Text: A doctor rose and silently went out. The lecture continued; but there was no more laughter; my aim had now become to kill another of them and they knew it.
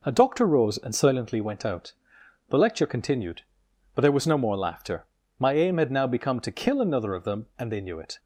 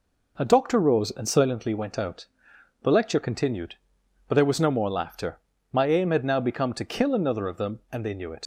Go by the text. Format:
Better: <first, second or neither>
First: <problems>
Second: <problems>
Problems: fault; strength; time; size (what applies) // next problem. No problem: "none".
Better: first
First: none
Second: leaves "it" unfinished; at 8.4 s; 70 ms